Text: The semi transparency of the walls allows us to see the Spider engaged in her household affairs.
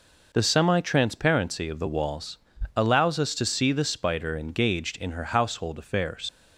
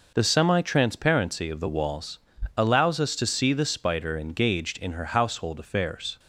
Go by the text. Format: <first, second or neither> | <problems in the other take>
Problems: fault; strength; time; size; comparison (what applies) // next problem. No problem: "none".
second | pauses between "walls" and "allows"; slight; at 2.3 s; 0.36 s long; slight in the second // leaves "affairs" unfinished; at 6.2 s; 90 ms